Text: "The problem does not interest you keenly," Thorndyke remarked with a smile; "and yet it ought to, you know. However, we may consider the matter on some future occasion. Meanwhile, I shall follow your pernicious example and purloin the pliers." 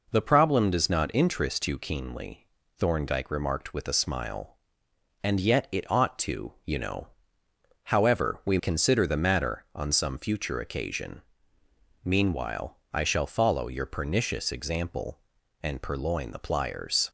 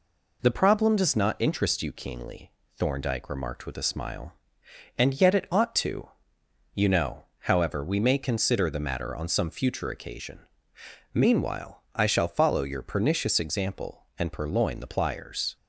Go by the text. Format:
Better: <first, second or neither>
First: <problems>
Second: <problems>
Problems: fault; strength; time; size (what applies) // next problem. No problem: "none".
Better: second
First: skips "may"; at 8.5 s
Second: none